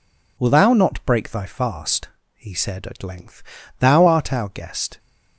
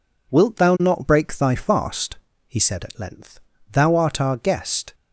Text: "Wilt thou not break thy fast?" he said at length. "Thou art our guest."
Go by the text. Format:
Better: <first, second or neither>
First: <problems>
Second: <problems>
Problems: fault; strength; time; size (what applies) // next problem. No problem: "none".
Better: second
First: says "Will" for "Wilt"; at 0.3 s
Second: none